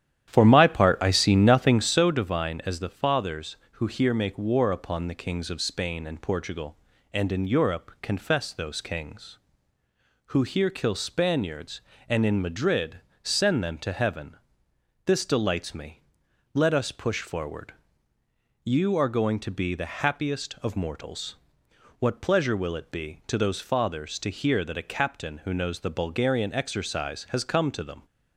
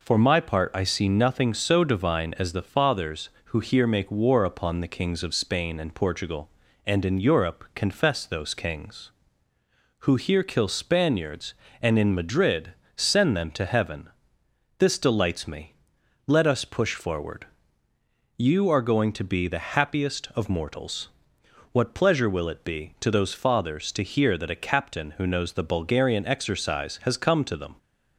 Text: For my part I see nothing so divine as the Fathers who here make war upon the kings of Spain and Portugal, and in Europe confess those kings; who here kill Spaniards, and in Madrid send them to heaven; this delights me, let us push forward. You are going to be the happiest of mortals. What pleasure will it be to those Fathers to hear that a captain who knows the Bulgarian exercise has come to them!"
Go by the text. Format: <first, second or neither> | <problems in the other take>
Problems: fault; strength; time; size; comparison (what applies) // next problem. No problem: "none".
second | starts louder than the rest; strong; until 2.1 s; 11 dB // pauses between "Madrid" and "send"; slight; at 12.9 s; 0.24 s long; slight in the second